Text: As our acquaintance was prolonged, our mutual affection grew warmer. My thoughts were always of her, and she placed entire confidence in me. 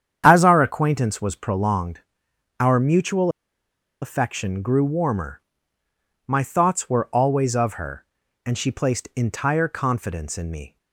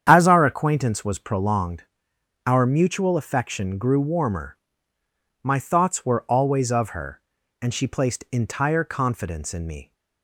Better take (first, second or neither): second